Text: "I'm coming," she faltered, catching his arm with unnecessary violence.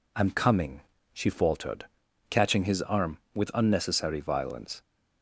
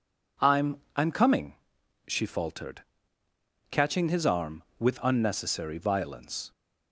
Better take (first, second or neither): first